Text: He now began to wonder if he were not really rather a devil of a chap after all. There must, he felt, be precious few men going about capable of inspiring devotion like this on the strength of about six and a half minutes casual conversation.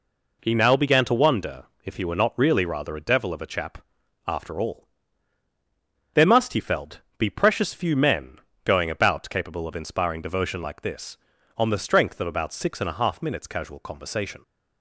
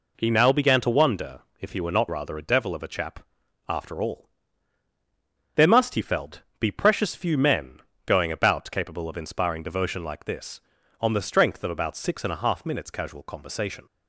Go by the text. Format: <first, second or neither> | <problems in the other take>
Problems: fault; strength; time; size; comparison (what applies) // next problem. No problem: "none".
first | pauses between "wonder" and "if"; slight; at 1.4 s; 0.20 s long; slight in the first // skips "really"; at 2.0 s // pauses between "chap" and "after"; noticeable; at 3.1 s; 0.48 s long; noticeable in the first // pauses between "men" and "going"; slight; at 7.7 s; 0.26 s long; slight in the first